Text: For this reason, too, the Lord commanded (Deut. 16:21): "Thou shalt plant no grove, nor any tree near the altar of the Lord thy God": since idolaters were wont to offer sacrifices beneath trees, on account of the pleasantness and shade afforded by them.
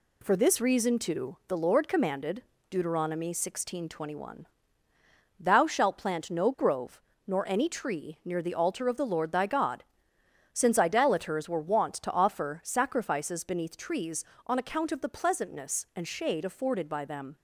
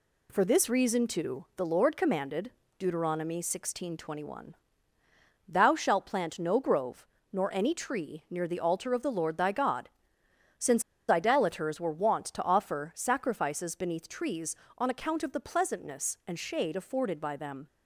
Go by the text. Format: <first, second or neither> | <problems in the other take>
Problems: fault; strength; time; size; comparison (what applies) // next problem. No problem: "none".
first | pauses between "since" and "idolaters"; slight; at 10.8 s; 0.28 s long